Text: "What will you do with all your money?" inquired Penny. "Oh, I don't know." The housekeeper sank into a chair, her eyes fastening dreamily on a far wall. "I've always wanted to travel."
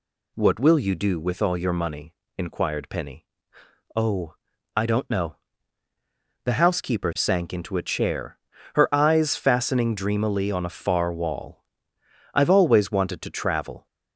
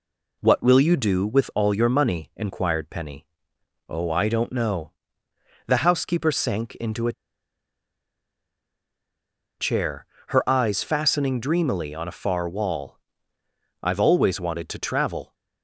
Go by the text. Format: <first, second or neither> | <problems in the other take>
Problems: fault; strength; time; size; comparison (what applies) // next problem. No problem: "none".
first | pauses between "a" and "chair"; strong; at 7.1 s; 2.4 s long